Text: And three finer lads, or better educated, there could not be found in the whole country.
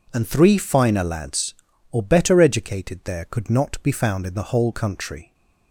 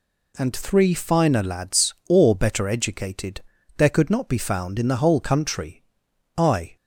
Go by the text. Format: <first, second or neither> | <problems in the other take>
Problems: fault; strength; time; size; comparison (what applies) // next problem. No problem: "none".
first | goes on to say "I"; slight; from 6.3 s on; 0.38 s long